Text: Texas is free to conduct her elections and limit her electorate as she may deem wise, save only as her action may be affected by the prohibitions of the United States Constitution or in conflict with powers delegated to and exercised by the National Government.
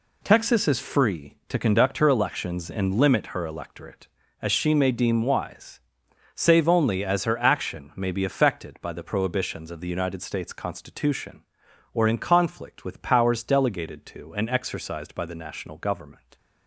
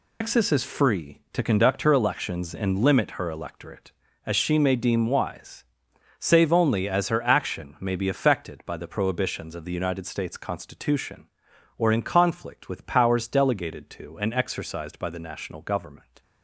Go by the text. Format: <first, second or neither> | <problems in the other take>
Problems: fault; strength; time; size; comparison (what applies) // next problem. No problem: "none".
first | loses the start of "Texas"; at 0.2 s; 130 ms